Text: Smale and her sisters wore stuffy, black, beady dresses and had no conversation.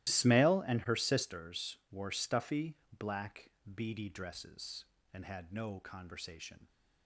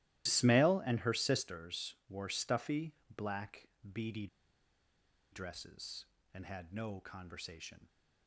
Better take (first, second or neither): first